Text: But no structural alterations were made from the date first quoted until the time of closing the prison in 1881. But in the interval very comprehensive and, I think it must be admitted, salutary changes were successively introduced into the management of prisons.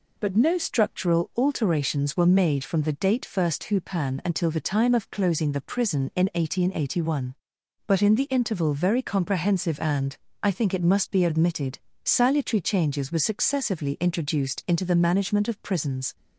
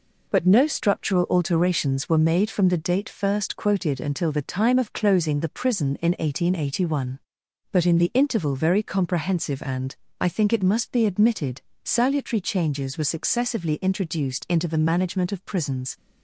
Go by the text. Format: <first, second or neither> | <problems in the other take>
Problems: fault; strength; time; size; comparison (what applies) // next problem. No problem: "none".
second | says "hupan" for "quoted"; at 3.6 s